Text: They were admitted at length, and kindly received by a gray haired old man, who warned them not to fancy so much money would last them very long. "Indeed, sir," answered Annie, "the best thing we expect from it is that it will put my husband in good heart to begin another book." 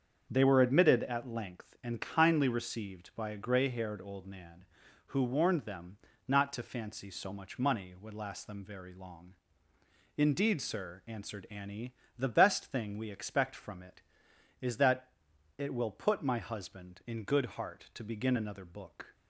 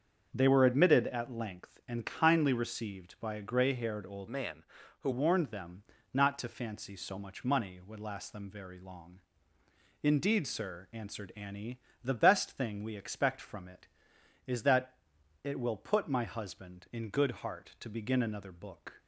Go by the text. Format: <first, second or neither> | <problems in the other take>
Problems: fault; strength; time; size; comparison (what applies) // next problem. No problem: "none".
first | starts louder than the rest; until 1.3 s; 7 dB; also in the first // changes voice from "man" to "who"; from 4.2 to 5.0 s; 0.8 s long // pauses between "them" and "not"; slight; at 5.8 s; 0.28 s long; slight in the first // pauses between "that" and "it"; at 14.9 s; 0.44 s long; also in the first